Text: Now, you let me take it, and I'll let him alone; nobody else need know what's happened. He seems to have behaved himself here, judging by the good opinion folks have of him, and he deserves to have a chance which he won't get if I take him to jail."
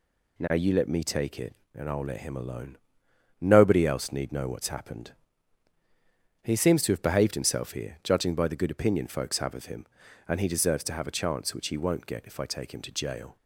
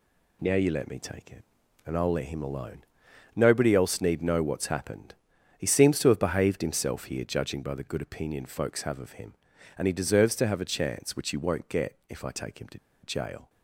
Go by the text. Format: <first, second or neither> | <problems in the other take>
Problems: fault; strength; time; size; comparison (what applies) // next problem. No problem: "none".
first | pauses between "to" and "jail"; slight; at 12.7 s; 0.25 s long